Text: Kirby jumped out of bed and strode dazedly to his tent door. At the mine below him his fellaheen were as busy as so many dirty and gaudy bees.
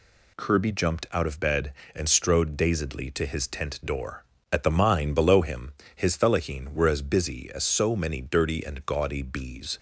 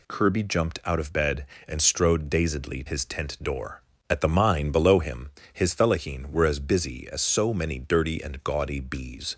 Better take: first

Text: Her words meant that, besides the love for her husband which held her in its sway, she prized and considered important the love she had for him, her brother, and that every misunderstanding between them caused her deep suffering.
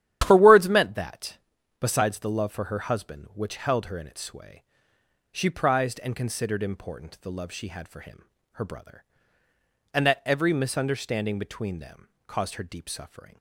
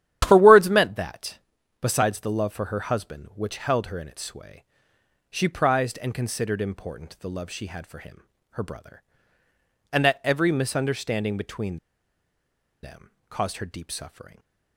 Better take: first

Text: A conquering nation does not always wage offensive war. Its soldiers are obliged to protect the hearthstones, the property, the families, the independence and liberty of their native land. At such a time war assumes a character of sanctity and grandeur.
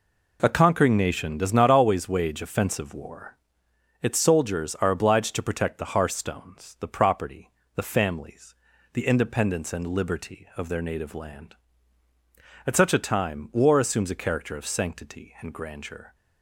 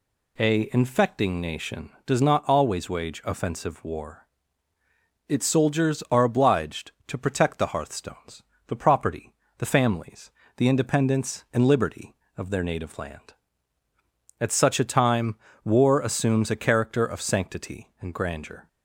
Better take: first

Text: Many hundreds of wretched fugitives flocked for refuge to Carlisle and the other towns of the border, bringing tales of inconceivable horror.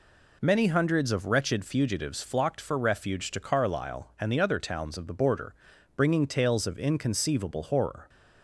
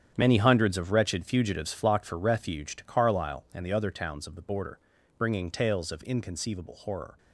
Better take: first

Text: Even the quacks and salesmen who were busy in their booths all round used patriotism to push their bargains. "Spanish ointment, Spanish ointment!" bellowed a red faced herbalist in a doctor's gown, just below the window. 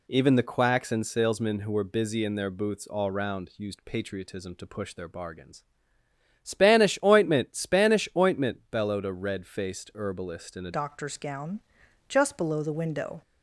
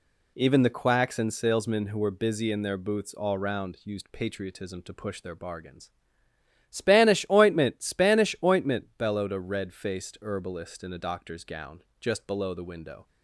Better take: second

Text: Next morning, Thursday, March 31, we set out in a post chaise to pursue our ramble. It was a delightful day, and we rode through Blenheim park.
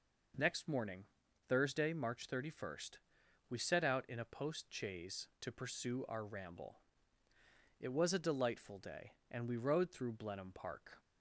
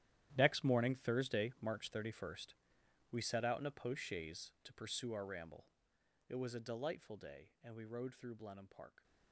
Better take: first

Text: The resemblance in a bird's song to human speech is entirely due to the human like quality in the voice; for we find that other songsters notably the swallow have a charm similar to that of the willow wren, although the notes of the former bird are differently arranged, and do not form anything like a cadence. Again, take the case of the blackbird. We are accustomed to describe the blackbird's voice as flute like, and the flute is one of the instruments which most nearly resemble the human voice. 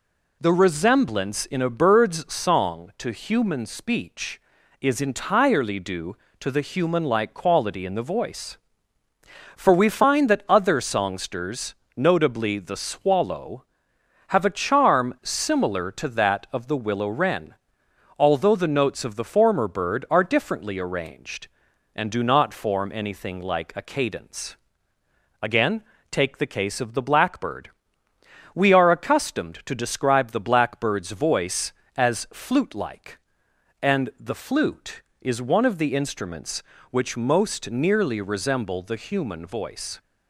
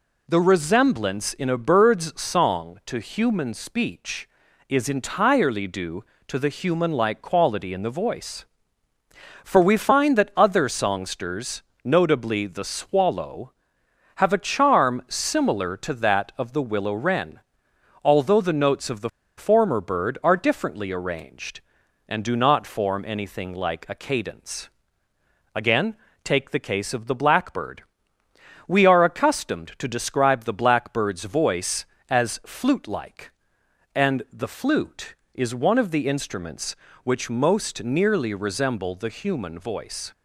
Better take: first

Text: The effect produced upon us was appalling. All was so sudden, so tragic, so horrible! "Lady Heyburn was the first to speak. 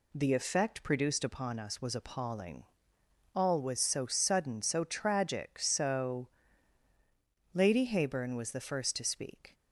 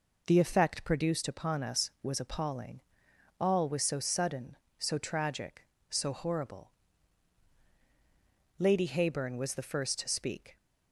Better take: second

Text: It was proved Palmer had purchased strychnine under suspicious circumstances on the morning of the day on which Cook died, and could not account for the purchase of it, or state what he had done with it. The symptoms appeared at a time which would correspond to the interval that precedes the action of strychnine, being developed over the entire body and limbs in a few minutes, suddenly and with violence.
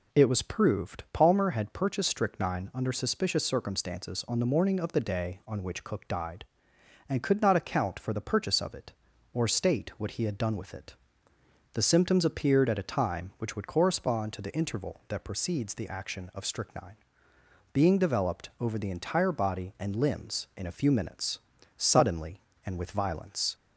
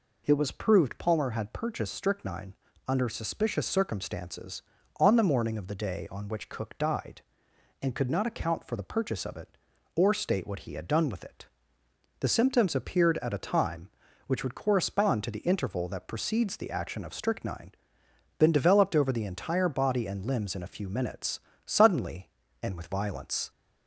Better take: first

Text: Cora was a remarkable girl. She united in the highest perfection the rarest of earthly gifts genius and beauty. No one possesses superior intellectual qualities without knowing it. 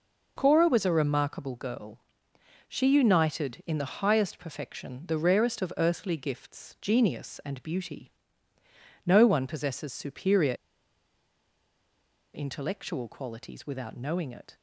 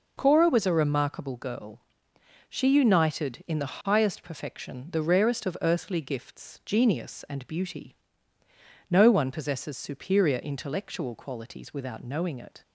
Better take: second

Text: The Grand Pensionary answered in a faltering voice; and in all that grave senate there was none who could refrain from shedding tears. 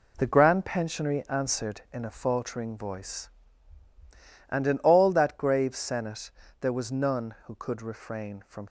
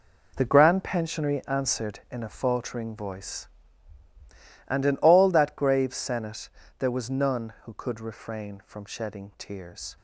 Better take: second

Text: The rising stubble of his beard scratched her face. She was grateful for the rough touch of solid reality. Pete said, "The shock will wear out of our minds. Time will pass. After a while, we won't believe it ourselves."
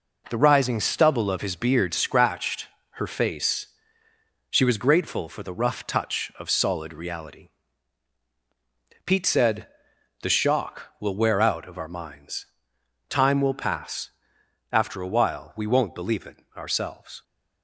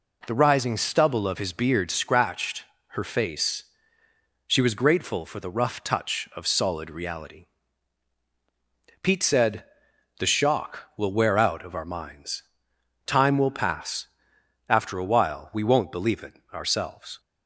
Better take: second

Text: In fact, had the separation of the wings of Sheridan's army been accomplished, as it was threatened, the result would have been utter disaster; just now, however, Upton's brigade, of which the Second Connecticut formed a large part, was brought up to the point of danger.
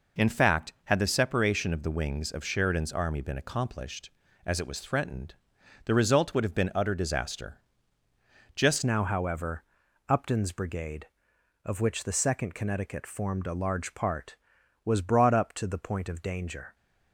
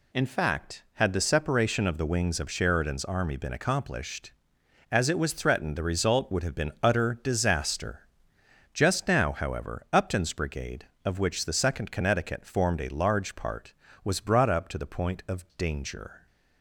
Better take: second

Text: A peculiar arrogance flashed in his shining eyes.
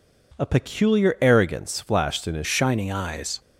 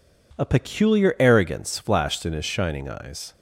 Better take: second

